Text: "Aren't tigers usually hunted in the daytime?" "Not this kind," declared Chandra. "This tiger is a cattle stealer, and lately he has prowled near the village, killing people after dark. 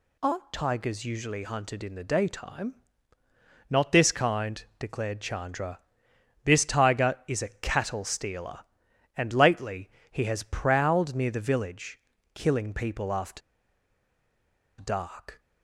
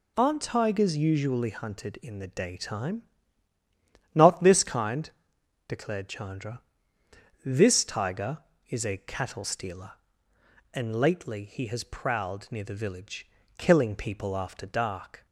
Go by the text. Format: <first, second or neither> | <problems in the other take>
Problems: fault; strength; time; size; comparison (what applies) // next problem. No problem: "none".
second | pauses between "lately" and "he"; slight; at 9.9 s; 0.18 s long // pauses between "after" and "dark"; strong; at 13.4 s; 1.4 s long